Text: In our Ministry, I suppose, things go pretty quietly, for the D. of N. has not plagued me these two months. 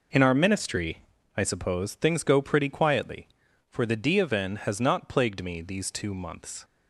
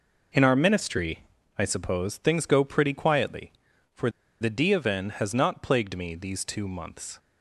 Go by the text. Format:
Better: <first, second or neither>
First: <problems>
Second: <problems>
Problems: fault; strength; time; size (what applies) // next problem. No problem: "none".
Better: first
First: none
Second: pauses between "for" and "the"; slight; at 4.0 s; 0.32 s long